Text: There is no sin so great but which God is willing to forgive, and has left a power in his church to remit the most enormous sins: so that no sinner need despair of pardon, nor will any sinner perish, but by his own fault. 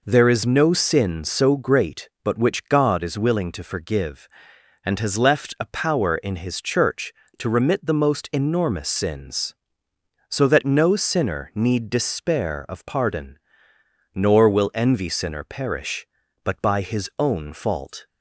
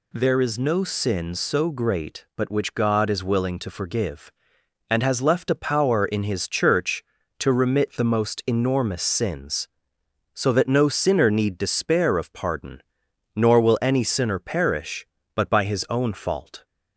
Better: second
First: says "envy" for "any"; at 14.7 s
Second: none

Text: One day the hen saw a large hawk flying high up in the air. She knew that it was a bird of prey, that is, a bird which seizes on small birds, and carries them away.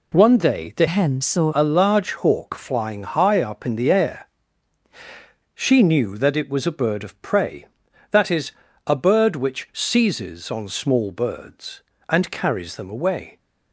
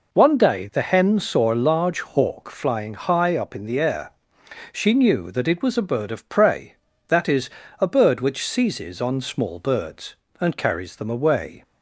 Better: second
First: changes voice from "hen" to "saw"; from 0.8 to 1.5 s; 0.7 s long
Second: none

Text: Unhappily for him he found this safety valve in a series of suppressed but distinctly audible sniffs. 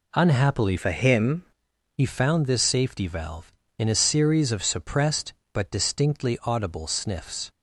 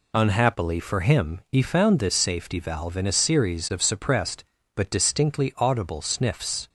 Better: second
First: changes voice from "for" to "him"; from 0.7 to 1.4 s; 0.7 s long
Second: none

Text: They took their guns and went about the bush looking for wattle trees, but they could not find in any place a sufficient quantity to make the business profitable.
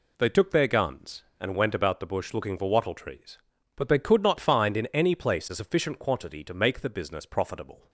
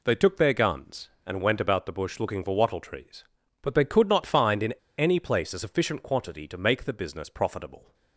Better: first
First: none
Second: pauses between "in" and "any"; slight; at 4.7 s; 0.24 s long

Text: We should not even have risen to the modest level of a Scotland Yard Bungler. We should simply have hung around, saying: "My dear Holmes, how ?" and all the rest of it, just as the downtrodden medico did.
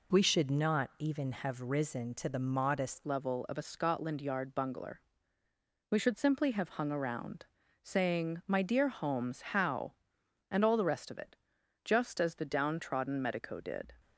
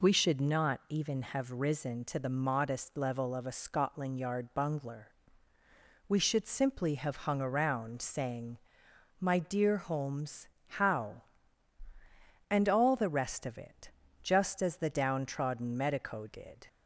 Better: second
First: changes voice at "level"; from 3.0 s on; 10.9 s long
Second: none

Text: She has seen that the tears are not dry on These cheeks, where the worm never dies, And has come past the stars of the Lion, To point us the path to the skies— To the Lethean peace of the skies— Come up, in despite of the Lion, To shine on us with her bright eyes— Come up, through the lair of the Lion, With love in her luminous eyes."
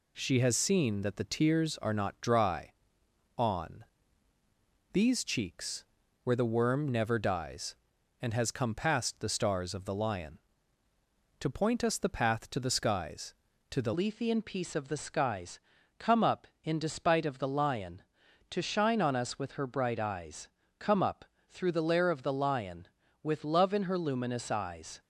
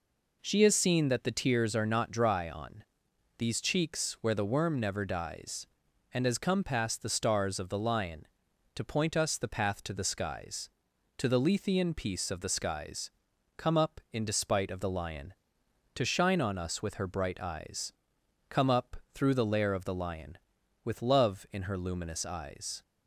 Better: second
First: pauses between "on" and "These"; at 3.8 s; 1.1 s long // changes voice at "Lethean"; from 13.9 s on; 11.0 s long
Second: pauses between "on" and "These"; noticeable; at 2.8 s; 0.54 s long

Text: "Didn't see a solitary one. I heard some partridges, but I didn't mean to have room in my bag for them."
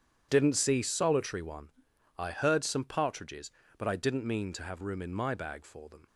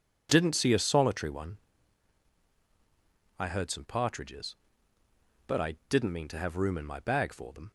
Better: second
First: starts louder than the rest; strong; until 1.3 s; 9 dB // skips "a"; at 0.8 s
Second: none

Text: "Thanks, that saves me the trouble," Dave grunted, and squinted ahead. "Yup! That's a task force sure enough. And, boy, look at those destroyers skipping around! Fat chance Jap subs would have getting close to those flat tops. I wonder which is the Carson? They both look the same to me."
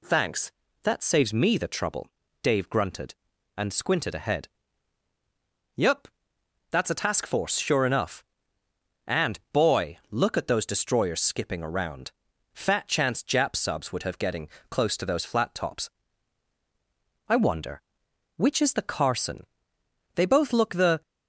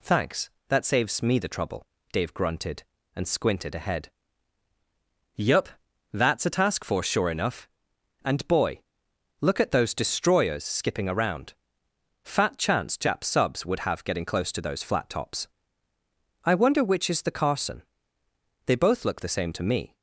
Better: second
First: pauses between "getting" and "close"; slight; at 14.4 s; 0.22 s long // stops before "same to me"; at 21.0 s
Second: none

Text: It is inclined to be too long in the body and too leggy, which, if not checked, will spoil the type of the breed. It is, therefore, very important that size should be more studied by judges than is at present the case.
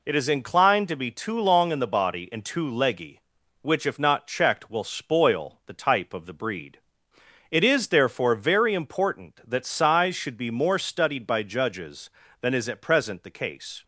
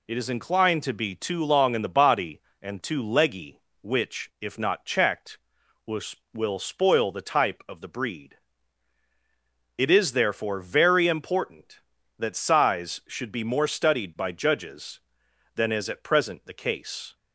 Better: first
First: none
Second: says "will" twice; at 6.3 s

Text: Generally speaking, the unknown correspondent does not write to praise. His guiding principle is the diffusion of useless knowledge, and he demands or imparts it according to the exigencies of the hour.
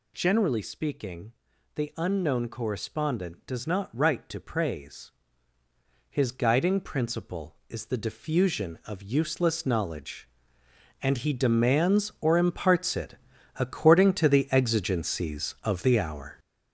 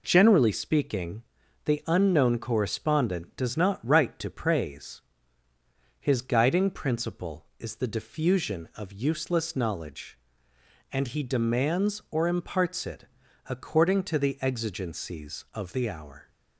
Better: second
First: gets louder; strong; throughout; 7.5 dB // pauses between "it" and "according"; at 13.1 s; 0.44 s long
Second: pauses between "it" and "according"; at 13.0 s; 0.44 s long

